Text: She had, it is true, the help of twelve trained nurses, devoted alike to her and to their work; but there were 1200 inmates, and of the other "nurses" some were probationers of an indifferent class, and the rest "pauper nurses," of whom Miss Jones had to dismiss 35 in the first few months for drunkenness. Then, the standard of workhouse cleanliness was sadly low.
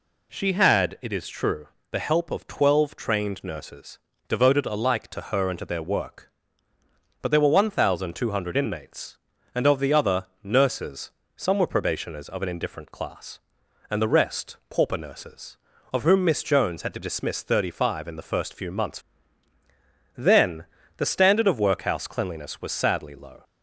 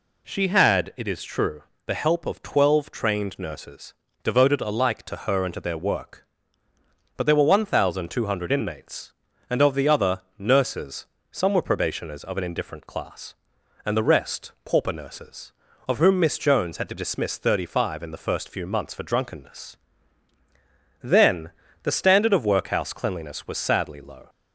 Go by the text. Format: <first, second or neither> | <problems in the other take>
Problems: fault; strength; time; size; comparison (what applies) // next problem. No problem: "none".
second | pauses between "nurses" and "some"; slight; at 11.1 s; 0.24 s long; slight in the second // skips "for drunkenness"; at 19.5 s